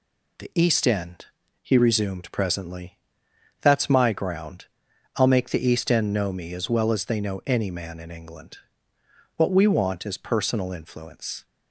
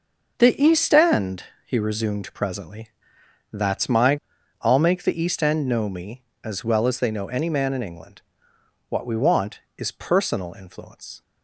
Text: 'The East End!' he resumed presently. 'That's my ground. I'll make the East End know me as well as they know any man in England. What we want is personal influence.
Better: first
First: none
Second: starts louder than the rest; until 1.3 s; 6.5 dB // skips "ground"; at 4.3 s

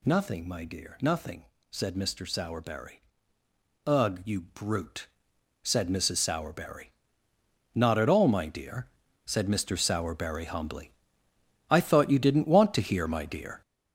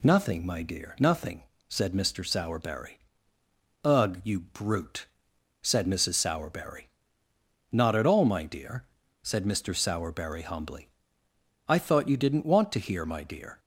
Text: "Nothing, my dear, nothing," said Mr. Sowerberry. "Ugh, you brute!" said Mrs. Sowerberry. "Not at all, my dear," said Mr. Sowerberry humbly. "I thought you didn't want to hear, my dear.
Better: second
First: gets louder; strong; throughout; 7.5 dB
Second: none

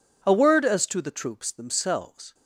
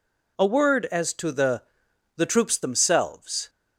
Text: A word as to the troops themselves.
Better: first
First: none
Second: says "the" twice; at 2.1 s

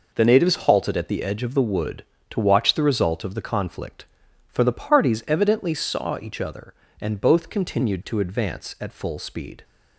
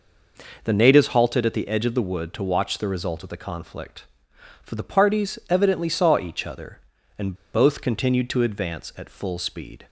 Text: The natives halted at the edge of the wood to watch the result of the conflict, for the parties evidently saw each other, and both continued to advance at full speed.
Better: first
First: none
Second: pauses between "and" and "both"; slight; at 7.3 s; 0.17 s long

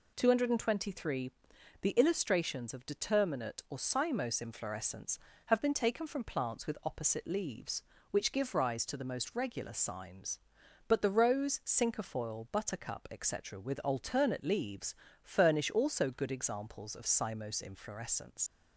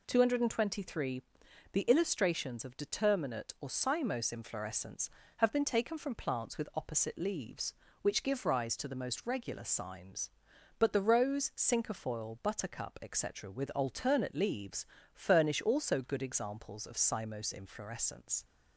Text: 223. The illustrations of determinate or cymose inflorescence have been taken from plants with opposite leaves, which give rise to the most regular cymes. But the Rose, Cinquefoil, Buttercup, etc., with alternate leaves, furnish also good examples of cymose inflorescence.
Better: second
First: leaves "inflorescence" unfinished; at 18.4 s; 70 ms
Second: none

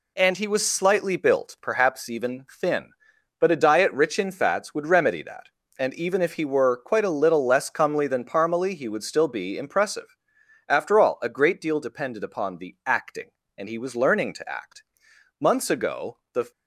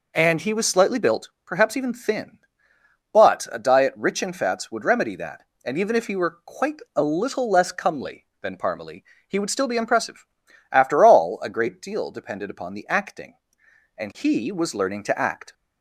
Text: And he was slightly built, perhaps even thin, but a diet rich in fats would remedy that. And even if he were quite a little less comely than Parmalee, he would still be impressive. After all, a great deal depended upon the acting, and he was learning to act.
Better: second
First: goes on to say "Months ago the"; noticeable; from 15.3 s on; 1.1 s long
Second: none

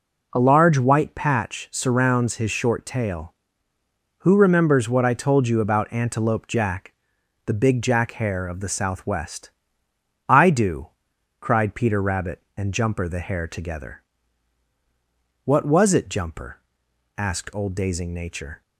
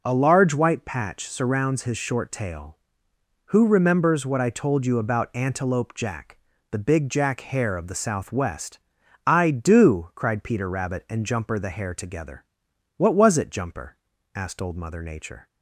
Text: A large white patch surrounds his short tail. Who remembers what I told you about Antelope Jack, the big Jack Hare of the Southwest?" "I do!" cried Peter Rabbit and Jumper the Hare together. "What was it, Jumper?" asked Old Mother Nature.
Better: second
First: says "Dazing" for "Mother"; at 17.7 s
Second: none

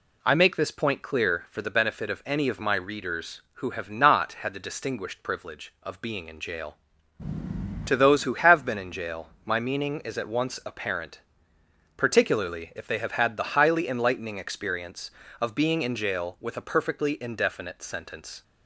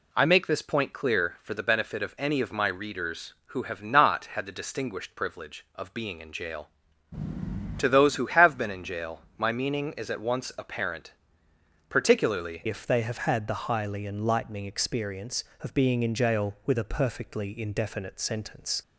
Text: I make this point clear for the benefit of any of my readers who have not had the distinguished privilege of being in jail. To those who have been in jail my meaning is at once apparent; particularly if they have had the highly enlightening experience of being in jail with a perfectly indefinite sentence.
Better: first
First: pauses between "jail" and "my"; slight; at 9.2 s; 0.16 s long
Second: pauses between "jail" and "my"; slight; at 9.2 s; 0.16 s long // changes voice at "if"; from 12.6 s on; 6.2 s long

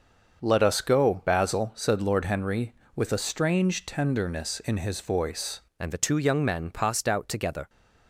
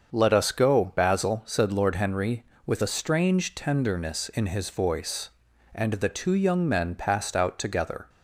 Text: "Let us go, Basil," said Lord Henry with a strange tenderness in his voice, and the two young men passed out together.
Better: second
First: starts louder than the rest; until 1.4 s; 6.5 dB // changes voice at "and"; from 5.7 s on; 1.9 s long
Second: starts louder than the rest; until 1.1 s; 7 dB

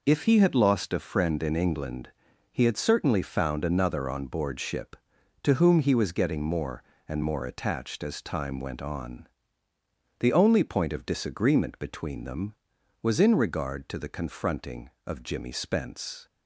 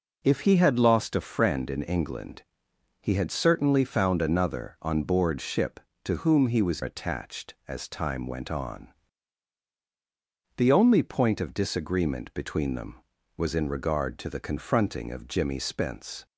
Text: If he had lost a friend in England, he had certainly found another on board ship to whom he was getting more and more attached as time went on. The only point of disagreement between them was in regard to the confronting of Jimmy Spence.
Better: first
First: none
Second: skips "getting more and more"; at 6.8 s

